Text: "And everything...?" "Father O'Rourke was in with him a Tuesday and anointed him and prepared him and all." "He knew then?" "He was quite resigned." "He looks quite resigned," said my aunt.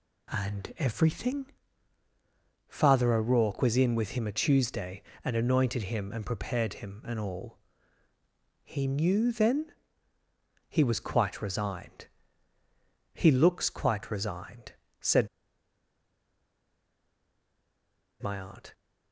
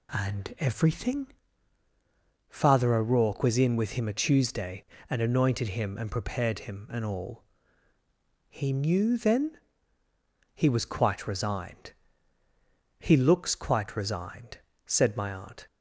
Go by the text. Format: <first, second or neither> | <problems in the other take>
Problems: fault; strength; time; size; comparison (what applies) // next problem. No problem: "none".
second | pauses between "said" and "my"; strong; at 15.2 s; 2.9 s long